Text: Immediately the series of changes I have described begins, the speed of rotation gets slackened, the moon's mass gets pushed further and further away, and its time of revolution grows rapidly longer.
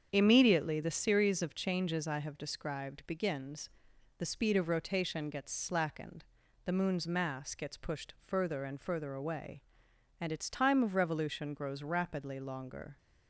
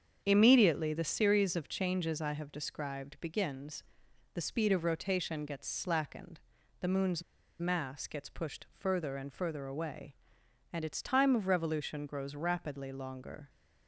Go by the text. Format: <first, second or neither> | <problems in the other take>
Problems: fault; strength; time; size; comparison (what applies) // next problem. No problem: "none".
first | starts louder than the rest; strong; until 1.2 s; 7.5 dB; strong in the first // pauses between "moon's" and "mass"; at 7.2 s; 0.38 s long